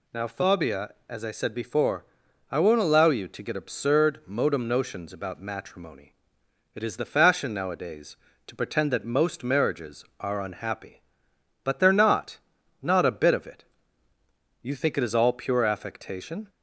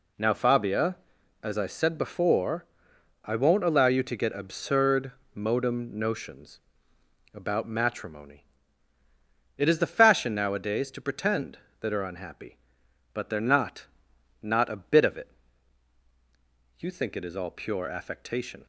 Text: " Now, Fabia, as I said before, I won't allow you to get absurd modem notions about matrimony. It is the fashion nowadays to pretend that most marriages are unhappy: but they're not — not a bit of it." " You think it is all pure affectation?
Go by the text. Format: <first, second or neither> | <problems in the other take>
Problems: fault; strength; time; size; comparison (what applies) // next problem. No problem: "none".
first | pauses between "absurd" and "modem"; slight; at 5.1 s; 0.22 s long // pauses between "notions" and "about"; noticeable; at 6.6 s; 0.72 s long // skips "most marriages"; at 11.9 s